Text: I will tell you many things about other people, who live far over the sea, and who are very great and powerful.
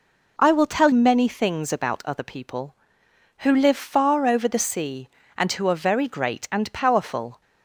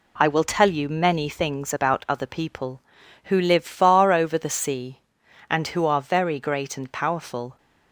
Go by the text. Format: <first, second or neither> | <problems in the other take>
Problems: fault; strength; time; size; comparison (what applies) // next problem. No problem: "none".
second | skips "you"; at 0.9 s